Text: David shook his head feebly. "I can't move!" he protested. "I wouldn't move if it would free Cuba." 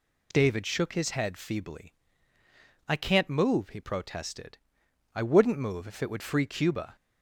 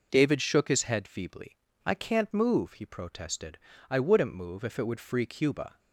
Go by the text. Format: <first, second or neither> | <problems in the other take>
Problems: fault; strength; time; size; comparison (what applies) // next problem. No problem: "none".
neither | none